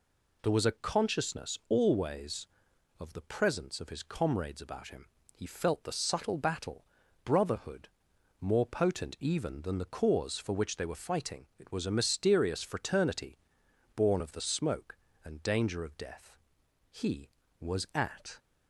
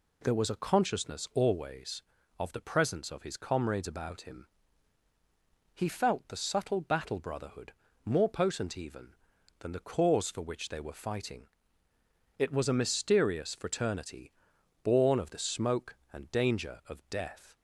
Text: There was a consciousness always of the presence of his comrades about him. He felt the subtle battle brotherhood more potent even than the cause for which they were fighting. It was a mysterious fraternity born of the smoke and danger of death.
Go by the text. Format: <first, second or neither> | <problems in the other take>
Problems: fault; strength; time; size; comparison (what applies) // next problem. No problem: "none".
second | pauses between "battle" and "brotherhood"; at 6.8 s; 0.40 s long // pauses between "brotherhood" and "more"; noticeable; at 7.8 s; 0.52 s long; slight in the second // pauses between "fraternity" and "born"; noticeable; at 13.3 s; 0.58 s long; noticeable in the second // goes on to say "He was at"; from 16.9 s on; 1.4 s long